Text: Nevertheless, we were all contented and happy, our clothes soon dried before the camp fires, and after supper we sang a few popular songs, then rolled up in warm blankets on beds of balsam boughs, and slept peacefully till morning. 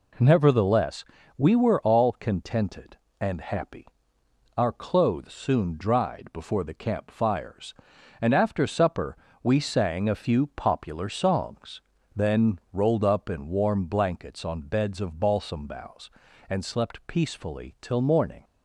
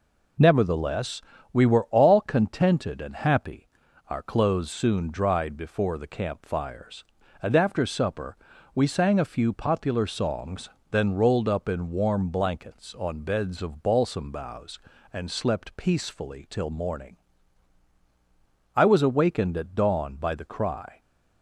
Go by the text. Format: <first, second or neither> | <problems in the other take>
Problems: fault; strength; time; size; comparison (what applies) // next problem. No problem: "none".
first | pauses between "supper" and "we"; at 8.3 s; 0.38 s long; slight in the first // goes on to say "I was awakened at dawn by the cry"; strong; from 18.7 s on; 2.2 s long